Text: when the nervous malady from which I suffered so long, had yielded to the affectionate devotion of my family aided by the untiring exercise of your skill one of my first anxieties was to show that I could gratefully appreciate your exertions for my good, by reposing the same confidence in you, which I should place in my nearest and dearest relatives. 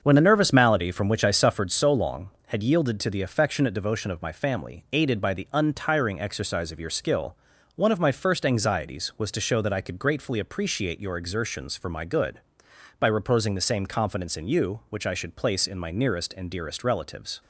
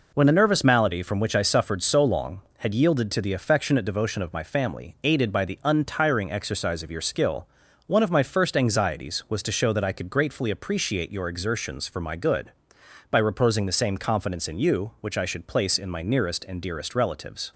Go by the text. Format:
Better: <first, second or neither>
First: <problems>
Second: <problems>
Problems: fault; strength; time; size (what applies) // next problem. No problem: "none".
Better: second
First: starts louder than the rest; until 1.7 s; 6.5 dB // pauses between "skill" and "one"; at 7.3 s; 0.40 s long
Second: pauses between "skill" and "one"; at 7.4 s; 0.40 s long